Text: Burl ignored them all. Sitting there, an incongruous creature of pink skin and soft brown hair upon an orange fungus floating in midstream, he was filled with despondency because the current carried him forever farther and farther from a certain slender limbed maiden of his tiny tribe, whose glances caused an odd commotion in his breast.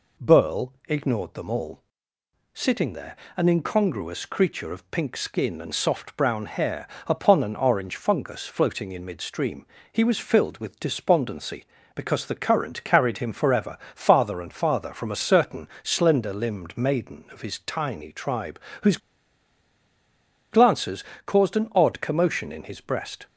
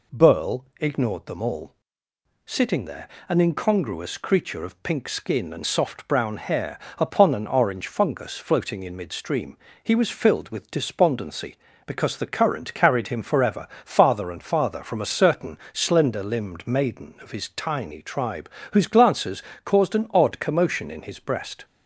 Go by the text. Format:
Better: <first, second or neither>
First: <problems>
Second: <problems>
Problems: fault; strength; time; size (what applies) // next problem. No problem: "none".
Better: second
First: pauses between "hair" and "upon"; slight; at 6.8 s; 0.18 s long // pauses between "forever" and "farther"; slight; at 13.7 s; 0.16 s long // pauses between "certain" and "slender"; slight; at 15.6 s; 0.16 s long // pauses between "whose" and "glances"; strong; at 18.9 s; 1.5 s long // pauses between "glances" and "caused"; slight; at 21.0 s; 0.22 s long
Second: pauses between "hair" and "upon"; slight; at 6.7 s; 0.18 s long // pauses between "forever" and "farther"; slight; at 13.6 s; 0.16 s long // pauses between "certain" and "slender"; slight; at 15.5 s; 0.16 s long // pauses between "glances" and "caused"; slight; at 19.4 s; 0.22 s long